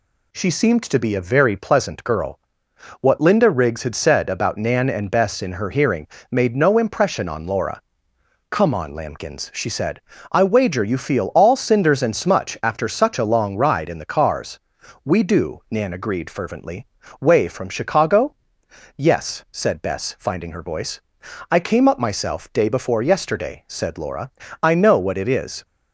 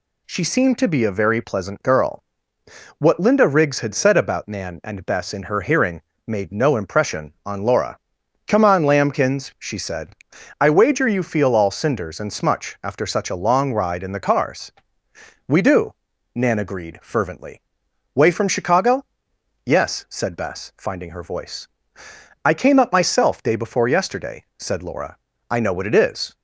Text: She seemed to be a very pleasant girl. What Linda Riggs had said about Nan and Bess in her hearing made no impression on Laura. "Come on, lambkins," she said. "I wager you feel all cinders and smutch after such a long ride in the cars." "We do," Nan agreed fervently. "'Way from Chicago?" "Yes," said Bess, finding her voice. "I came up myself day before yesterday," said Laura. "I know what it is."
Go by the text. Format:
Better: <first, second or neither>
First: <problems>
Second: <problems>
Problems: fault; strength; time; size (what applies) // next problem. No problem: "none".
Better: neither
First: pauses between "hearing" and "made"; slight; at 6.0 s; 0.24 s long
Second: pauses between "hearing" and "made"; slight; at 6.0 s; 0.26 s long